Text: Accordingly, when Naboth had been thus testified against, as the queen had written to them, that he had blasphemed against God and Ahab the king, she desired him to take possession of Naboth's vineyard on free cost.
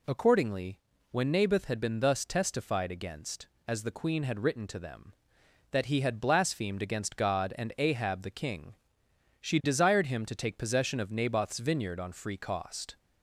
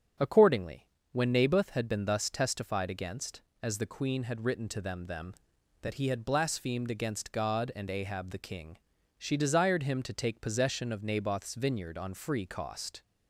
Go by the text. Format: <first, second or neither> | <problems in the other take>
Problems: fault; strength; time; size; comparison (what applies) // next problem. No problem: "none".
first | starts louder than the rest; strong; until 1.4 s; 7.5 dB // says "them" twice; at 5.0 s